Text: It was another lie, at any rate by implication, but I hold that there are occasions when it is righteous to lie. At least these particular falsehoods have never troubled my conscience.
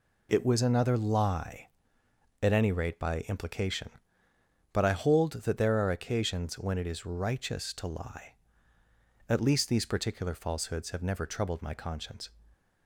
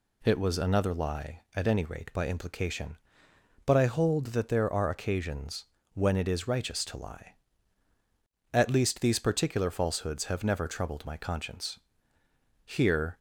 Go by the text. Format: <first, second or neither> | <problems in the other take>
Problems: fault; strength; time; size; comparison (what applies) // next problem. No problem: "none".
first | pauses between "occasions" and "when"; slight; at 5.6 s; 0.28 s long // goes on to say "Here"; from 12.6 s on; 0.52 s long